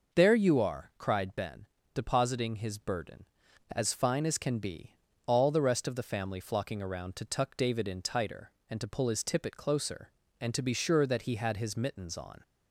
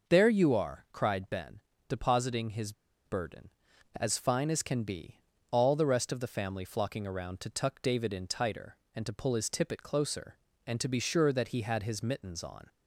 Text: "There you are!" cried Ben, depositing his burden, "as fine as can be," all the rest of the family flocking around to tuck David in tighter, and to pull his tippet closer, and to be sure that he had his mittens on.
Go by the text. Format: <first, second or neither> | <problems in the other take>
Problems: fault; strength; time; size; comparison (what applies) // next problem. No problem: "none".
first | pauses between "his" and "burden"; slight; at 2.7 s; 0.33 s long